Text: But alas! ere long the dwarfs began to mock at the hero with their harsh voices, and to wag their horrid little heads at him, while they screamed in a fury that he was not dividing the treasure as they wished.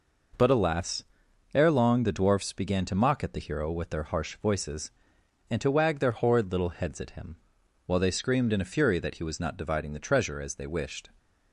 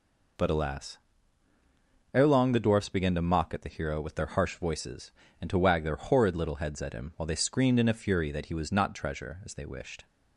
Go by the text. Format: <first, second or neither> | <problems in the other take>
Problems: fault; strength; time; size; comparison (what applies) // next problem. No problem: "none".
first | skips "dividing the"; at 8.9 s